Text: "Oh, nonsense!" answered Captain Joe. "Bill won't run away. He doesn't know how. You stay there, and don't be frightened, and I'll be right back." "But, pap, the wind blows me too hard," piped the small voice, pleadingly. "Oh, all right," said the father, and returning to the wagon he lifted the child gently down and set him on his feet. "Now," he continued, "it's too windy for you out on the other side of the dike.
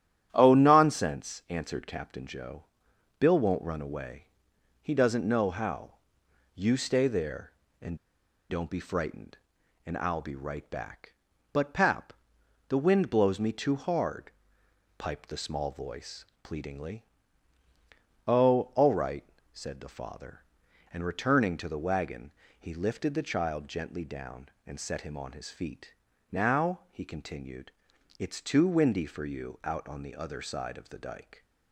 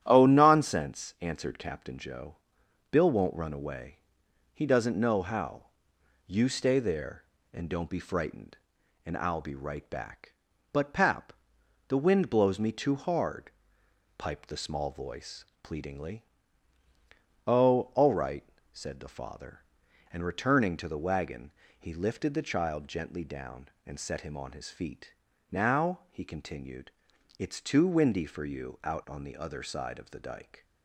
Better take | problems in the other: second | starts louder than the rest; strong; until 1.3 s; 11 dB; strong in the second // pauses between "and" and "don't"; noticeable; at 7.9 s; 0.52 s long // pauses between "wagon" and "he"; slight; at 22.3 s; 0.28 s long; slight in the second

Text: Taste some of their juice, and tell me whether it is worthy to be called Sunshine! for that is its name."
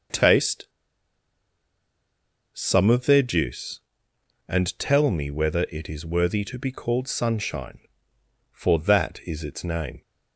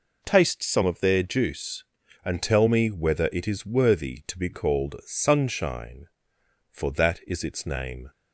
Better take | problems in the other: second | pauses between "Taste" and "some"; strong; at 0.6 s; 1.8 s long

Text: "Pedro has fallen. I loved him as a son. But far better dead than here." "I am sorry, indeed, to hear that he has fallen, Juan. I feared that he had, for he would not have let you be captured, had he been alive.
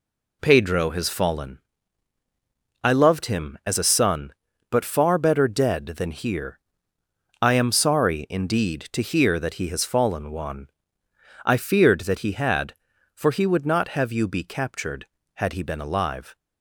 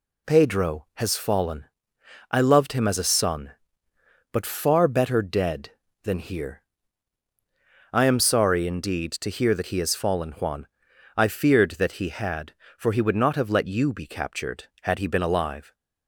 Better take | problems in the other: second | skips "let"; at 14.1 s

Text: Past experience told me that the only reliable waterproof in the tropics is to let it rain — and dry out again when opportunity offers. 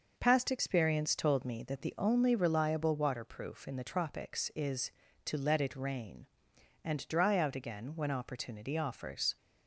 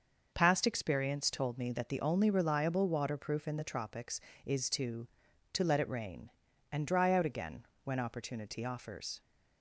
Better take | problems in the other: first | starts louder than the rest; noticeable; until 1.3 s; 6 dB // says "to" twice; at 5.5 s // pauses between "again" and "when"; slight; at 7.6 s; 0.20 s long

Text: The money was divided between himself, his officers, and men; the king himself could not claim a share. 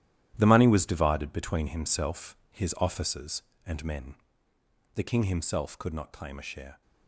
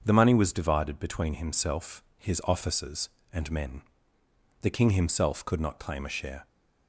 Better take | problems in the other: second | gets quieter; strong; throughout; 11.5 dB // starts louder than the rest; strong; until 1.3 s; 12.5 dB; also in the second

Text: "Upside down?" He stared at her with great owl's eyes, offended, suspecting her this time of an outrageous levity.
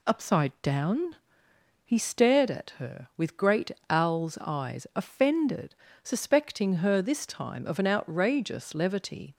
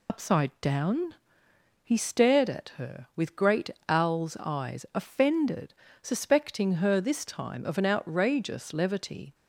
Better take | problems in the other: first | loses the start of "Upside"; at 0.0 s; 70 ms // pauses between "great" and "owl's"; slight; at 3.6 s; 0.18 s long; slight in the first

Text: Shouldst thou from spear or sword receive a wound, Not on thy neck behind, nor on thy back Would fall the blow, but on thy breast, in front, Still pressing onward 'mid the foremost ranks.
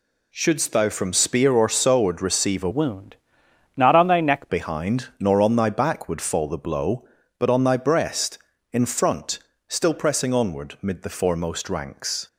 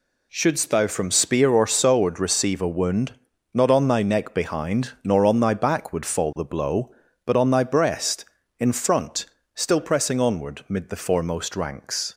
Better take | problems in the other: second | changes voice from "wound" to "neck"; from 2.7 to 4.4 s; 1.7 s long

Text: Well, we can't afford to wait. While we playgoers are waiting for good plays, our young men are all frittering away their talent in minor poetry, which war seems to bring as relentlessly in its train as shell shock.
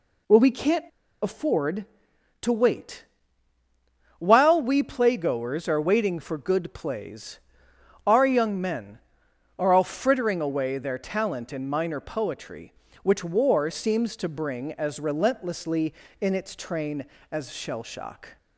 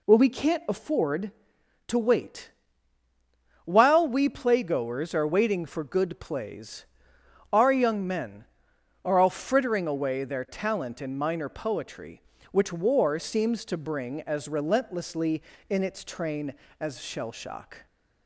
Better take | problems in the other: second | pauses between "can't" and "afford"; at 0.8 s; 0.37 s long

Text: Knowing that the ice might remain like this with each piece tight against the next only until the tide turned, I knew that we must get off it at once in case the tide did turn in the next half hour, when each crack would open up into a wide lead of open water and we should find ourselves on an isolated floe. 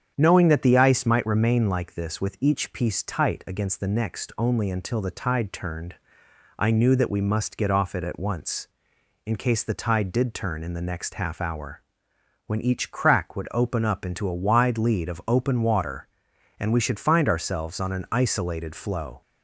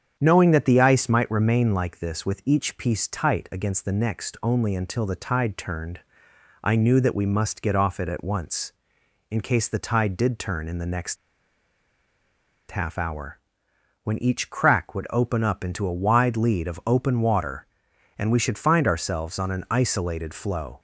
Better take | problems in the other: first | starts louder than the rest; strong; until 1.2 s; 8 dB; strong in the first // pauses between "next" and "half"; strong; at 11.1 s; 1.5 s long

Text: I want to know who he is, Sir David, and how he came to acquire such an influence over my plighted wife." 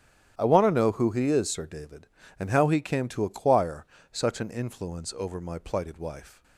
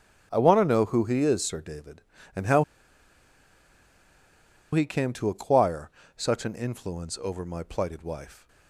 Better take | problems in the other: first | starts louder than the rest; strong; until 1.3 s; 11 dB; strong in the first // pauses between "how" and "he"; strong; at 2.6 s; 2.0 s long // pauses between "acquire" and "such"; slight; at 5.8 s; 0.26 s long; slight in the first

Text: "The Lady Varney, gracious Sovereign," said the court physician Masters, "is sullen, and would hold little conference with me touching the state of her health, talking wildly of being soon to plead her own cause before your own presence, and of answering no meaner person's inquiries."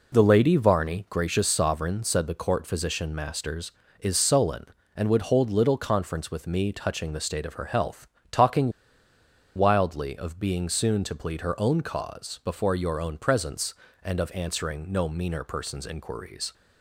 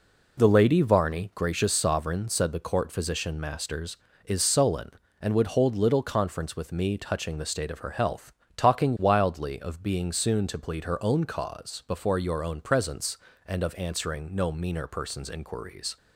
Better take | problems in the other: second | pauses between "talking" and "wildly"; noticeable; at 8.7 s; 0.85 s long

